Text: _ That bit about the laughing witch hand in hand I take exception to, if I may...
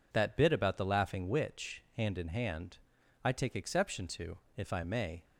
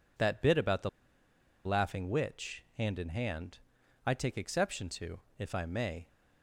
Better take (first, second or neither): first